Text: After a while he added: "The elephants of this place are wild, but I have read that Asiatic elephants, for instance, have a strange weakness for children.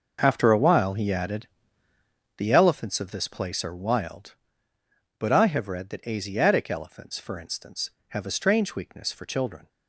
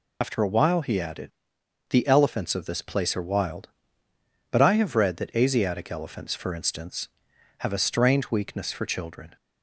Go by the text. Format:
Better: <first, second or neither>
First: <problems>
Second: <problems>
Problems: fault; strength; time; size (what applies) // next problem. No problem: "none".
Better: first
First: none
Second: loses the start of "After"; at 0.2 s; 90 ms